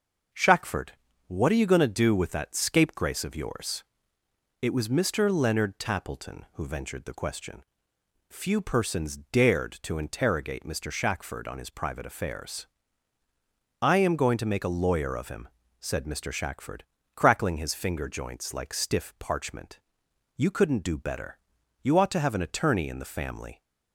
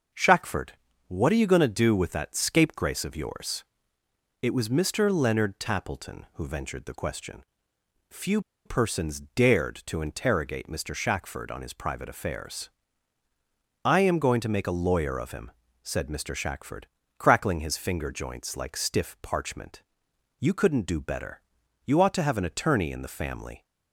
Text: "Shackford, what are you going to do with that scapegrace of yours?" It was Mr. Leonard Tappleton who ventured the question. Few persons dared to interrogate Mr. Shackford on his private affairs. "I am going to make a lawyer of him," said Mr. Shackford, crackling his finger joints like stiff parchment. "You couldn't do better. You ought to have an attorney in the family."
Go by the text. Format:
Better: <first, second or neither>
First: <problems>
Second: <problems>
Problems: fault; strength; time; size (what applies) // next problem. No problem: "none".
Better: first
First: starts louder than the rest; noticeable; until 1.6 s; 6 dB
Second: starts louder than the rest; noticeable; until 1.4 s; 6 dB // pauses between "Few" and "persons"; slight; at 8.3 s; 0.25 s long